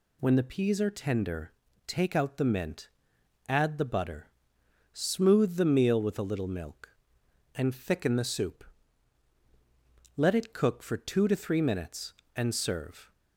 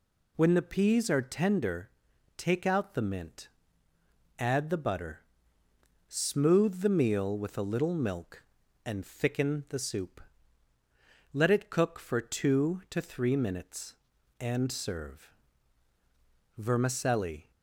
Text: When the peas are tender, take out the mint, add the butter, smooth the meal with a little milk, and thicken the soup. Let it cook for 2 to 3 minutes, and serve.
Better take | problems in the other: first | goes on to say "VERMICELLI"; noticeable; from 16.5 s on; 0.92 s long

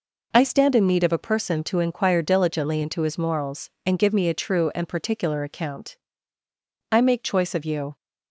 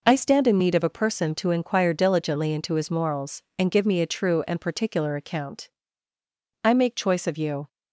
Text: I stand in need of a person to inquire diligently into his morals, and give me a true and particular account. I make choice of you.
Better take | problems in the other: neither | none

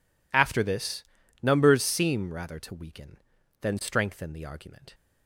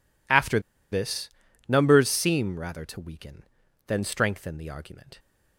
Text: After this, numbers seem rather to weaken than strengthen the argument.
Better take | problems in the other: first | pauses between "After" and "this"; slight; at 0.5 s; 0.32 s long

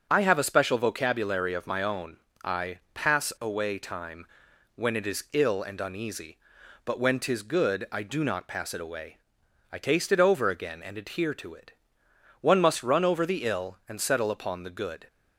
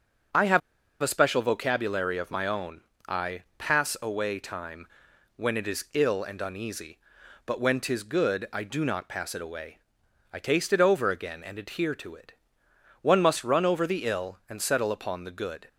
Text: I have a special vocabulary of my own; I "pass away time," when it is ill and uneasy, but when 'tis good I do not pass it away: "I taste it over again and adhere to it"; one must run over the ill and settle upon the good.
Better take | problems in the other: first | starts louder than the rest; strong; until 1.7 s; 7.5 dB; strong in the first // pauses between "have" and "a"; at 0.6 s; 0.41 s long

